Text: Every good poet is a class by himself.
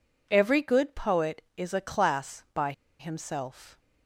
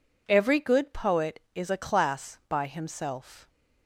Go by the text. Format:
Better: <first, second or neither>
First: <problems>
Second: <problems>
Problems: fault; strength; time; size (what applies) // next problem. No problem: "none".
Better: second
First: pauses between "by" and "himself"; slight; at 2.7 s; 0.27 s long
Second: none